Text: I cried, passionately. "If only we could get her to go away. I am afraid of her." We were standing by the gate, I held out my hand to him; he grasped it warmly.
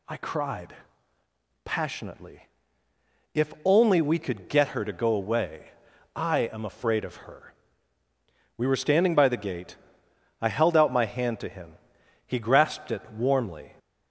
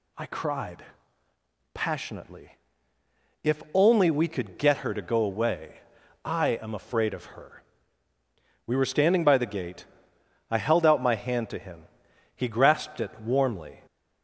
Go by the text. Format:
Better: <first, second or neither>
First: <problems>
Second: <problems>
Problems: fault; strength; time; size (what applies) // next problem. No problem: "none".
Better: neither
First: none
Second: none